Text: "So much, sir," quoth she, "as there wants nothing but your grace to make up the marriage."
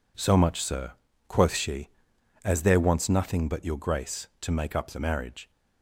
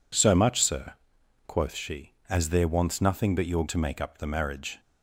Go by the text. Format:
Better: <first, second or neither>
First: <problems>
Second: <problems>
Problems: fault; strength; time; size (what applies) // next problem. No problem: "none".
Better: first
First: none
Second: skips "grace"; at 3.6 s